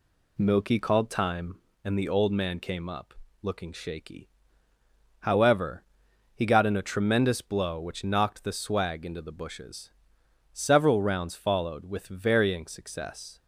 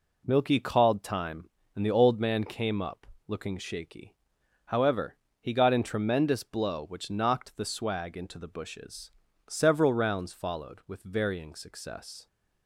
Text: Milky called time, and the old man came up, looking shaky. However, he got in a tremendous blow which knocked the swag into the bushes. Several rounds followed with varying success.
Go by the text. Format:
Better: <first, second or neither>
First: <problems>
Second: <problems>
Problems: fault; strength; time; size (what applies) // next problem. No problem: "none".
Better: first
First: none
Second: skips "a"; at 5.8 s